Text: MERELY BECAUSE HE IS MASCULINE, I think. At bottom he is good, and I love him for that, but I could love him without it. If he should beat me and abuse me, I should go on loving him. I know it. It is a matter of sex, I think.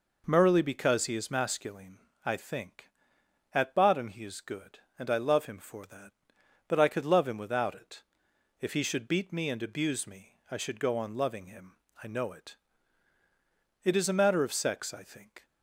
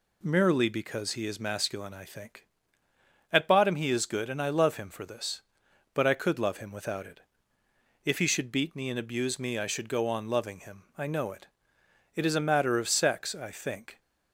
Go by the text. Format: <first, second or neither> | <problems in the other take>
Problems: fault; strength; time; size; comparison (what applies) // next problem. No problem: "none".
first | says "this" for "that"; at 5.0 s